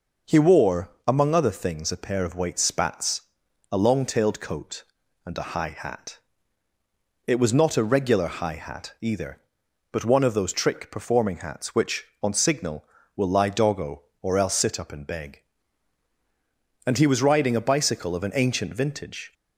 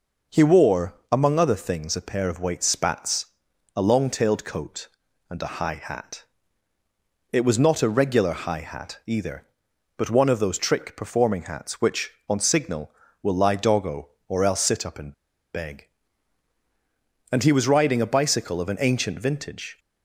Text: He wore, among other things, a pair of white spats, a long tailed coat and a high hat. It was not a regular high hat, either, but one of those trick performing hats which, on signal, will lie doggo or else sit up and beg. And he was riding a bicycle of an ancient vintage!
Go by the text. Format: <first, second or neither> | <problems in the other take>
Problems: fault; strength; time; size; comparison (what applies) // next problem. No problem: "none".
first | pauses between "and" and "beg"; at 15.1 s; 0.42 s long